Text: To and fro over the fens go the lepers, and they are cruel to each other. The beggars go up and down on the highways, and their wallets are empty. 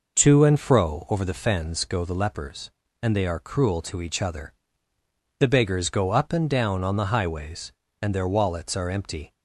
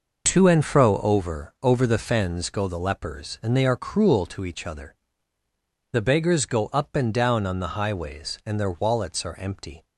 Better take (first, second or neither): first